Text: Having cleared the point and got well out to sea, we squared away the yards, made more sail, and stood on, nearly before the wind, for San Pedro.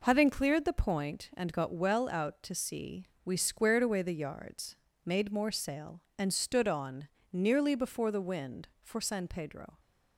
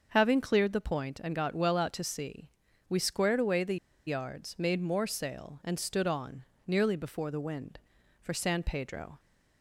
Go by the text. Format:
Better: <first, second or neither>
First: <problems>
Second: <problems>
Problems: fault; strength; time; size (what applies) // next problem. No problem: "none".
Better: first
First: none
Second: starts louder than the rest; until 1.1 s; 6.5 dB // pauses between "the" and "yards"; slight; at 3.7 s; 0.29 s long